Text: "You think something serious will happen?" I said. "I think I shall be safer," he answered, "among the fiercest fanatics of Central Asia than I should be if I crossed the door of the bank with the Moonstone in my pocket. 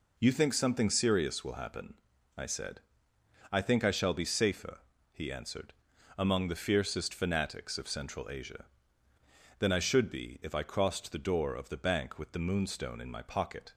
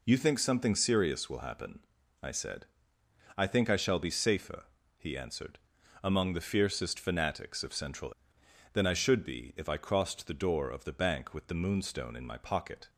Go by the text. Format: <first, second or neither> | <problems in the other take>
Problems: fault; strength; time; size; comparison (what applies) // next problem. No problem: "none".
first | skips "Asia"; at 8.4 s